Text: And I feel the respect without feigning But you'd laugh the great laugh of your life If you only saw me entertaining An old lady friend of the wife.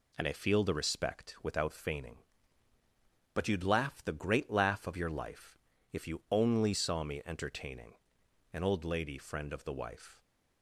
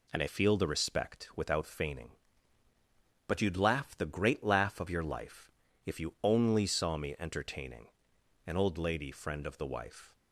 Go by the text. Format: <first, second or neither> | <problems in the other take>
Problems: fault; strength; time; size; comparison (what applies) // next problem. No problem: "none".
neither | pauses between "life" and "If"; slight; the same in both // pauses between "entertaining" and "An"; noticeable; the same in both